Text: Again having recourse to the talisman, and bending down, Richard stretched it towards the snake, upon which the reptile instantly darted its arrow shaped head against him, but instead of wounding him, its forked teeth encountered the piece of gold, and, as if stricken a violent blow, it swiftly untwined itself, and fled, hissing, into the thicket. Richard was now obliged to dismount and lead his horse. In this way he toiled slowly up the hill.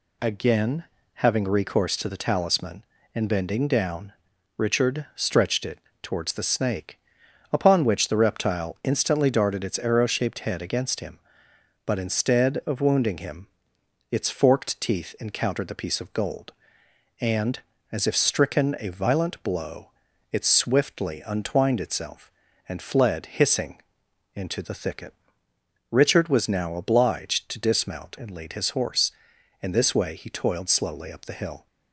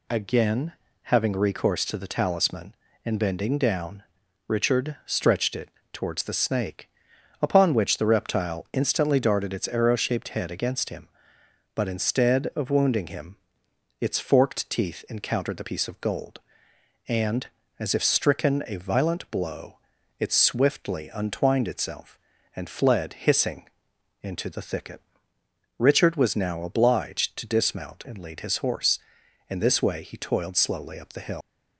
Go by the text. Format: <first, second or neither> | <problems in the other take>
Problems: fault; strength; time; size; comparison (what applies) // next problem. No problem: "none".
first | pauses between "Again" and "having"; slight; at 0.7 s; 0.30 s long; slight in the first // pauses between "it" and "towards"; slight; at 5.6 s; 0.24 s long; slight in the first // leaves "hill" unfinished; at 31.4 s; 130 ms